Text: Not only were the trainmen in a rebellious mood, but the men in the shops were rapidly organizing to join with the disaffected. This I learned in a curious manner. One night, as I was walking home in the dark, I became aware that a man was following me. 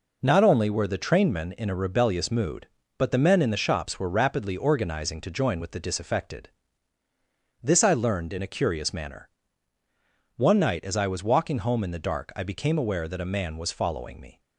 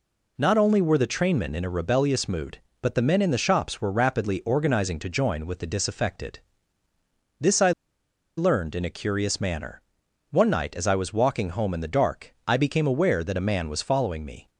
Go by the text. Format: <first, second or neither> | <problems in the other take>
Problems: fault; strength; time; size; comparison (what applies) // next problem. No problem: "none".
first | pauses between "I" and "learned"; noticeable; at 7.6 s; 0.67 s long